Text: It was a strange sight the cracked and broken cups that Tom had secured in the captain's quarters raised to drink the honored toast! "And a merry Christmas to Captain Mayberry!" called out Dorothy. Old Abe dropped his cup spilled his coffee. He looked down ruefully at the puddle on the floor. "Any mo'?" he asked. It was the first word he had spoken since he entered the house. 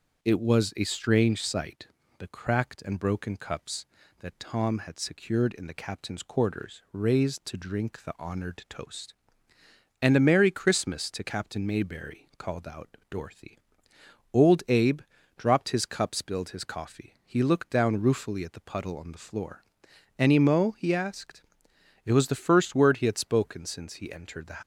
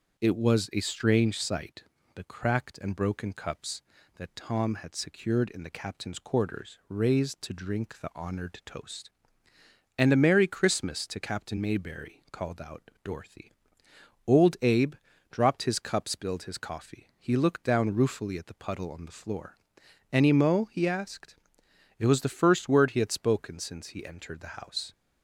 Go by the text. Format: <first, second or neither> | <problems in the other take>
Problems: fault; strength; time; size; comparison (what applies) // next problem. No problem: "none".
second | starts louder than the rest; until 1.2 s; 6.5 dB; also in the second // pauses between "sight" and "the"; slight; at 1.8 s; 0.32 s long; slight in the second // pauses between "Abe" and "dropped"; at 15.0 s; 0.38 s long; also in the second // stops before "house"; at 24.6 s